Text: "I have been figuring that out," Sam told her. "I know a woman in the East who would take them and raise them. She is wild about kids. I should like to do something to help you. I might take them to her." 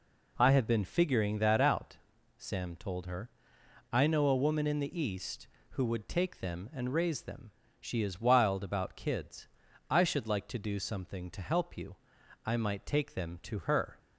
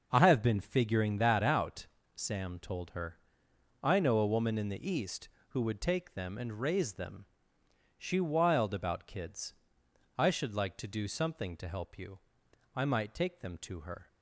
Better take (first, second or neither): first